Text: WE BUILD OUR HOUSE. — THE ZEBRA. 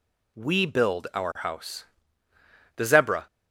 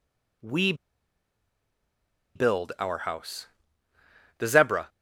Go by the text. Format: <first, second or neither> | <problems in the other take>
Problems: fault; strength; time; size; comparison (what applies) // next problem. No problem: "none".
first | pauses between "WE" and "BUILD"; strong; at 0.7 s; 1.6 s long